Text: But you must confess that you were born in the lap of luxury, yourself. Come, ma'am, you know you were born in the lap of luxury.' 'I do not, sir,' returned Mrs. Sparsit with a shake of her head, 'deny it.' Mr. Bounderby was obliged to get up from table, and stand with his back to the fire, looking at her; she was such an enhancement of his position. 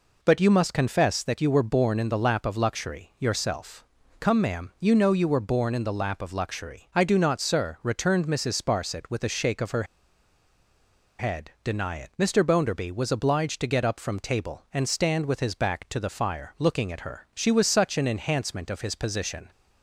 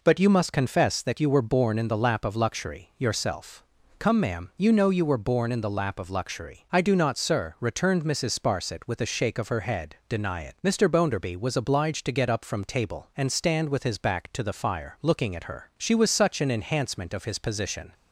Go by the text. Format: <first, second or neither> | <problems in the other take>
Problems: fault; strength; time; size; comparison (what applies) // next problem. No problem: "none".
second | pauses between "her" and "head"; strong; at 9.8 s; 1.3 s long